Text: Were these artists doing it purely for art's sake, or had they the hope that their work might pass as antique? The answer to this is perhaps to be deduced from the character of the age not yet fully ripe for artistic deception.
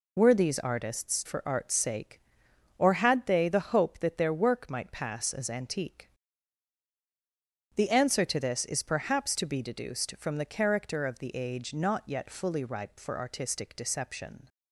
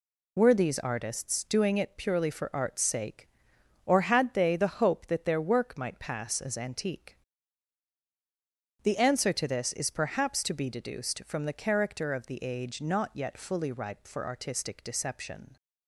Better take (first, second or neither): second